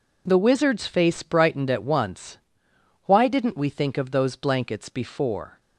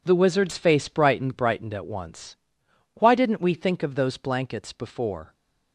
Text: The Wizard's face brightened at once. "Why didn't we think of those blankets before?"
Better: first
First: none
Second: says "brightened" twice; at 1.3 s

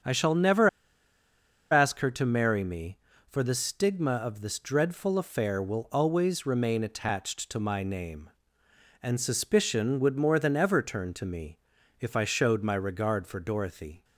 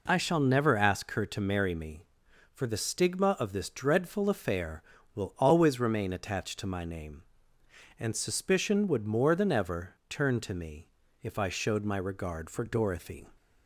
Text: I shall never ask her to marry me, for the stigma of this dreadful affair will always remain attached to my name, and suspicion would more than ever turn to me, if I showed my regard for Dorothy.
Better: second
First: starts louder than the rest; strong; until 2.0 s; 7.5 dB // pauses between "never" and "ask"; at 0.6 s; 1.0 s long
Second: none

